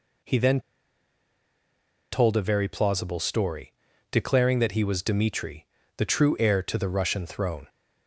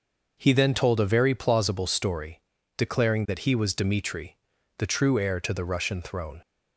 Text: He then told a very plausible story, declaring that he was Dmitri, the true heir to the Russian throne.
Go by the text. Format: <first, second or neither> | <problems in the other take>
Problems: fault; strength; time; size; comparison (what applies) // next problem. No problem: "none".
second | pauses between "then" and "told"; strong; at 0.6 s; 1.5 s long